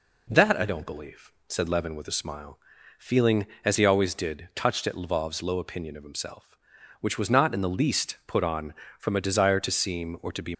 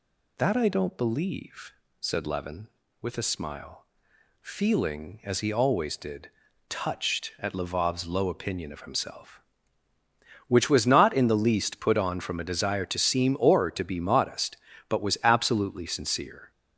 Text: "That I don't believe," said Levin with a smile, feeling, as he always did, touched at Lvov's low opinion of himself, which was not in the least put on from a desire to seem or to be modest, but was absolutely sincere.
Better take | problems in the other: second | stops before "modest but was absolutely sincere"; at 10.5 s

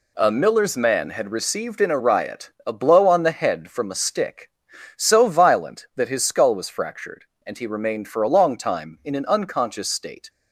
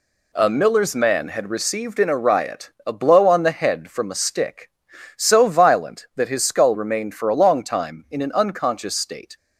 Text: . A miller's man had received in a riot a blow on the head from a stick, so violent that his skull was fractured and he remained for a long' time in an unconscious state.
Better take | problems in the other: first | pauses between "riot" and "a"; slight; at 2.7 s; 0.16 s long; slight in the first // skips "was fractured and he"; at 6.7 s

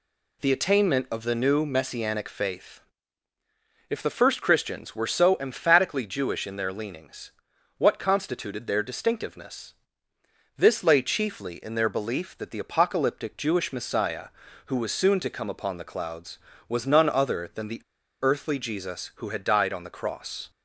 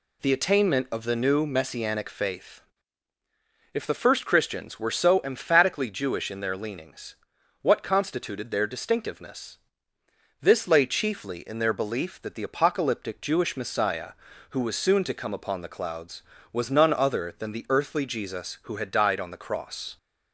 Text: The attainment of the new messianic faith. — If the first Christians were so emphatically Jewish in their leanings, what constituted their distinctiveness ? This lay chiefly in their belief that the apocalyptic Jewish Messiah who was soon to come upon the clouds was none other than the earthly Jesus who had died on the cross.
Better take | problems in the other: second | pauses between "the" and "earthly"; at 17.8 s; 0.41 s long

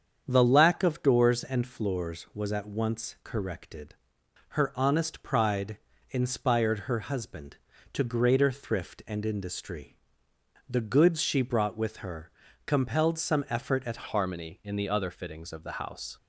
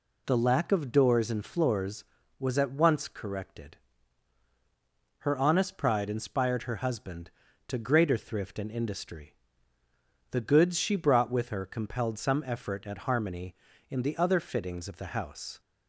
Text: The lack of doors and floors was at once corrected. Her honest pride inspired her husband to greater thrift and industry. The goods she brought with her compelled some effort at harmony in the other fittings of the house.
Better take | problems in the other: second | starts louder than the rest; strong; until 1.2 s; 7.5 dB // pauses between "pride" and "inspired"; slight; at 5.7 s; 0.32 s long // pauses between "her" and "compelled"; slight; at 12.3 s; 0.34 s long // changes voice at "harmony"; from 14.0 s on; 2.1 s long

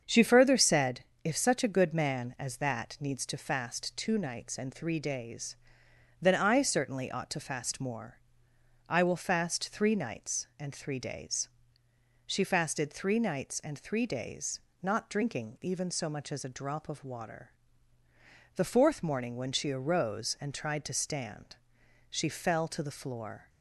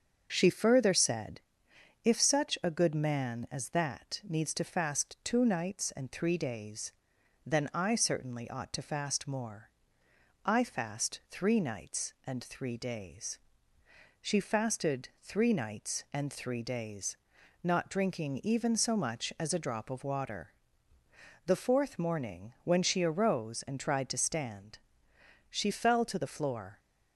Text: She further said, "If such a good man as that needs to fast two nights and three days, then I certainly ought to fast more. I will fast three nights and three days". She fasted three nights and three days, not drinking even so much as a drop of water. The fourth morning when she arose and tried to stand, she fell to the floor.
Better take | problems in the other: first | starts louder than the rest; until 1.3 s; 7 dB; strong in the first // skips "will"; at 10.6 s

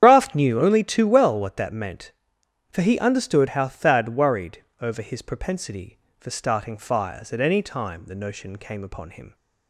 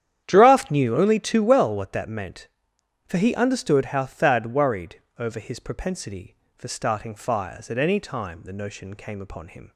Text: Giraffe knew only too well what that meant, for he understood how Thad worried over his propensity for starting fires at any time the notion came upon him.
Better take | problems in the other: second | loses the start of "Giraffe"; at 0.0 s; 140 ms // starts louder than the rest; strong; until 1.0 s; 9.5 dB; strong in the second // pauses between "worried" and "over"; slight; at 4.6 s; 0.18 s long; slight in the second

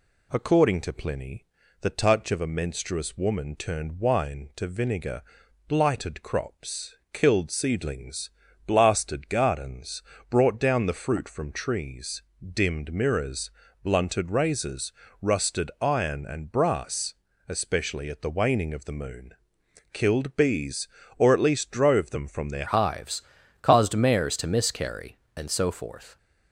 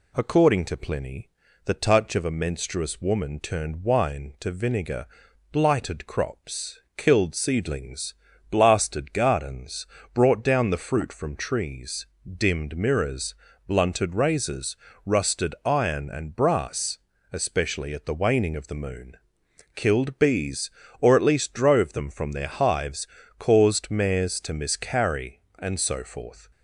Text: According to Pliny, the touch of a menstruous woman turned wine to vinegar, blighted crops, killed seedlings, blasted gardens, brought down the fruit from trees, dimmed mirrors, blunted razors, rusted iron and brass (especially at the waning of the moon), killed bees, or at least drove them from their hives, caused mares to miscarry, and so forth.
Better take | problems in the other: second | changes voice at "hives"; from 22.6 s on; 3.5 s long

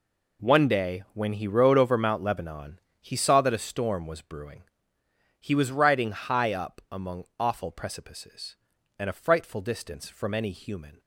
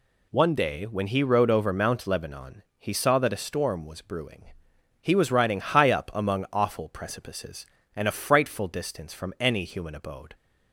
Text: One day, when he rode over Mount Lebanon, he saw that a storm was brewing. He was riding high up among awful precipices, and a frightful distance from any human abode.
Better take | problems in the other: second | stops before "abode"; at 11.0 s

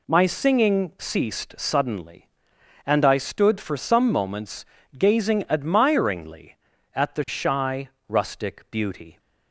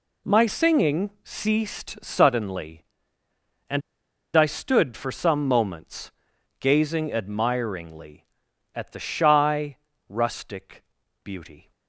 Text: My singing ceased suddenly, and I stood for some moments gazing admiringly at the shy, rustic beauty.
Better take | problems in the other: first | pauses between "and" and "I"; noticeable; at 3.8 s; 0.53 s long // pauses between "moments" and "gazing"; noticeable; at 6.1 s; 0.48 s long; slight in the first // pauses between "rustic" and "beauty"; at 10.8 s; 0.40 s long

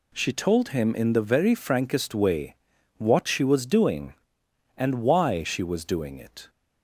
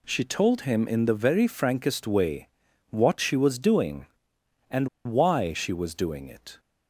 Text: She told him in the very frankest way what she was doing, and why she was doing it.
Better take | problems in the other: first | pauses between "way" and "what"; at 2.4 s; 0.42 s long; also in the first // pauses between "and" and "why"; slight; at 4.8 s; 0.16 s long

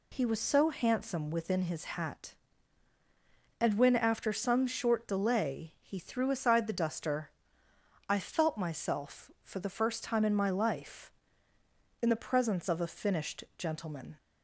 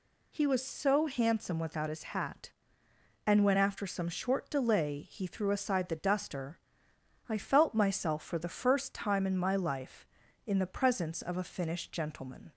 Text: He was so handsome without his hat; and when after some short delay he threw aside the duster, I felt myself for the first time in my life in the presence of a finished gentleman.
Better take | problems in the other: second | says "within" for "without"; at 1.3 s

